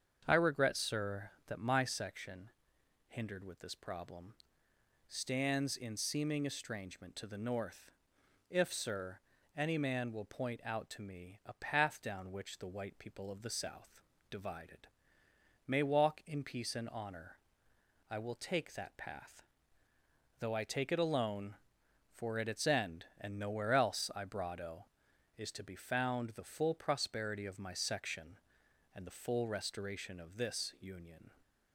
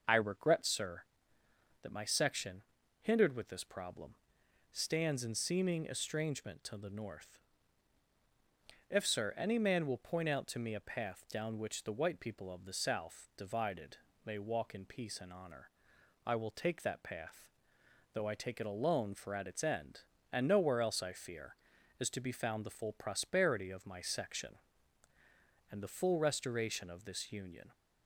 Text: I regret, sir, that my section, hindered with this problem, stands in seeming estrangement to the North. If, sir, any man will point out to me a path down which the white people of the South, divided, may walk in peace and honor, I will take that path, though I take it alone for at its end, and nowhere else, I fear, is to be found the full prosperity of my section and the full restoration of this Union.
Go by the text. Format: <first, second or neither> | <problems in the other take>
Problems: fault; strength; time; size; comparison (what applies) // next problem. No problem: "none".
second | starts louder than the rest; strong; until 1.2 s; 7 dB; noticeable in the second // says "brado" for "fear"; at 24.2 s